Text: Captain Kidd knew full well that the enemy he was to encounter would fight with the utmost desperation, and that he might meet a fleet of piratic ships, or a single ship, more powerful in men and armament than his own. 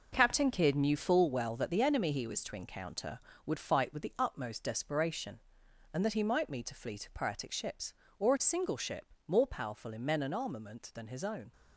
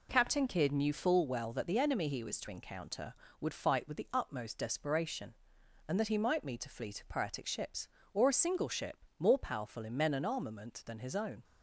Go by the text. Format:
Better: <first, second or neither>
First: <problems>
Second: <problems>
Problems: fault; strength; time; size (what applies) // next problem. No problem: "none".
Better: second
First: gets quieter; strong; throughout; 8 dB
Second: none